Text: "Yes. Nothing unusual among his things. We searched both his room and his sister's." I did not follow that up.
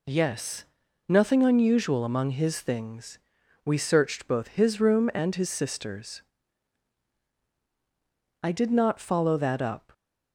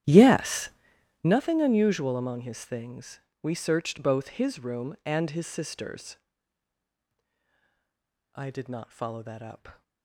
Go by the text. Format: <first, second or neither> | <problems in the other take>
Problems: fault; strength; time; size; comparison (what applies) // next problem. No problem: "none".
first | starts louder than the rest; strong; until 1.4 s; 11.5 dB